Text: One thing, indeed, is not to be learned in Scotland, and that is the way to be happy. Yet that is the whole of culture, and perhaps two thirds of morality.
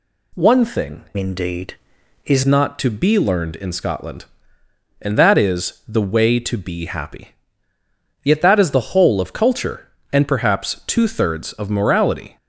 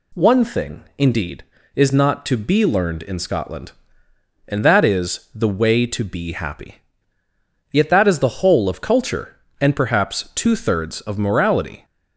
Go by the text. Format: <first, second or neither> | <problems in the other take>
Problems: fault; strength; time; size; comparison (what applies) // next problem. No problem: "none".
second | changes voice from "indeed" to "is"; from 1.1 to 2.4 s; 1.3 s long